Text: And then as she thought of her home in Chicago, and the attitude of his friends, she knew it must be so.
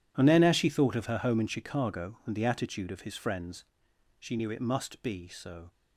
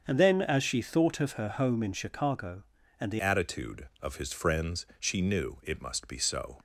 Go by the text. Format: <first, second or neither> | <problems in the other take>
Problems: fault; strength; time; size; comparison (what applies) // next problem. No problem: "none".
first | starts louder than the rest; until 1.0 s; 7 dB // changes voice at "attitude"; from 3.1 s on; 3.4 s long